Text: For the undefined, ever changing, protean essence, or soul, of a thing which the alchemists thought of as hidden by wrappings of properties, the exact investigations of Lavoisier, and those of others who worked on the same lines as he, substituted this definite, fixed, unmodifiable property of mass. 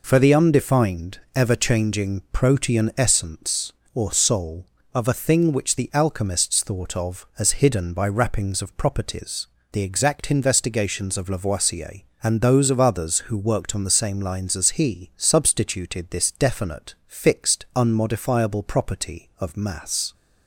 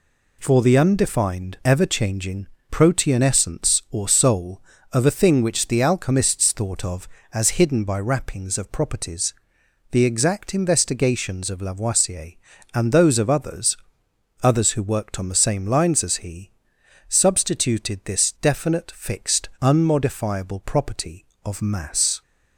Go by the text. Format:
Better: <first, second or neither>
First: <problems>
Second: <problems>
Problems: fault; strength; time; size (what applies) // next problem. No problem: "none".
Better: first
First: none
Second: says "others" twice; at 14.4 s